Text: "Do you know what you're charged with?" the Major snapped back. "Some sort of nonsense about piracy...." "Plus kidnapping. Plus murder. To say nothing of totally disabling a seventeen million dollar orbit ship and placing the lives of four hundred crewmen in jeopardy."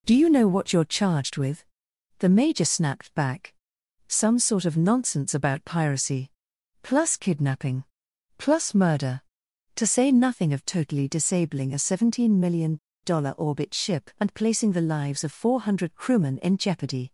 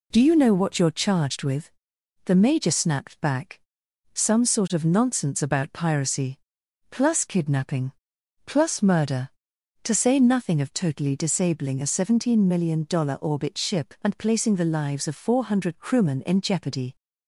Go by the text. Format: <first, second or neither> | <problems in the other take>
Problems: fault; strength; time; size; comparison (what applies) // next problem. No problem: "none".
second | pauses between "million" and "dollar"; slight; at 12.7 s; 0.28 s long